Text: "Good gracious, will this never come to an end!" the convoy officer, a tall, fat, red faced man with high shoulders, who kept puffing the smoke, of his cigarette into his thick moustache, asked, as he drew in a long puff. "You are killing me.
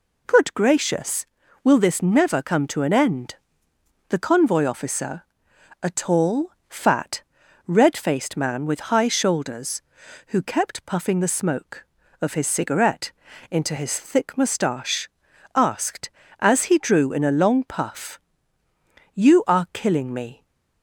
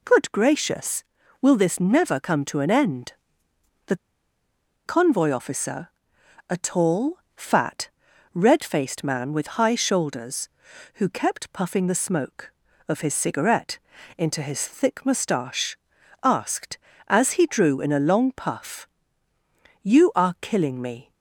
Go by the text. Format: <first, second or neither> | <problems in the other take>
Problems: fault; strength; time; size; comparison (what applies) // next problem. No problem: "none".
first | pauses between "the" and "convoy"; noticeable; at 3.9 s; 0.91 s long // pauses between "cigarette" and "into"; at 13.7 s; 0.38 s long; also in the first